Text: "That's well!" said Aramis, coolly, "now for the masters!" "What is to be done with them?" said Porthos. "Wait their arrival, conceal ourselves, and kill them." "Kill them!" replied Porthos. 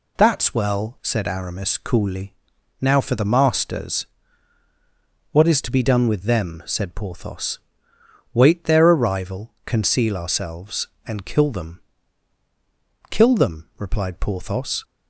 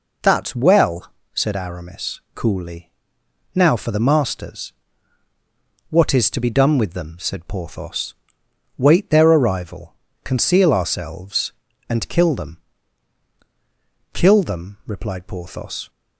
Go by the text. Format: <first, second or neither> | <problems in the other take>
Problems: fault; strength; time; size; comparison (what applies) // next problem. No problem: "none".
neither | none